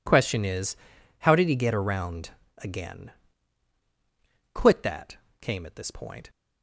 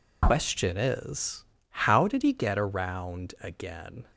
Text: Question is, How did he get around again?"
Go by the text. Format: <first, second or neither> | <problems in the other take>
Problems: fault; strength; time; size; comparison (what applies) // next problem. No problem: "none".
second | pauses between "around" and "again"; slight; at 2.2 s; 0.30 s long // goes on to say "Quit that came at this point"; strong; from 4.5 s on; 1.7 s long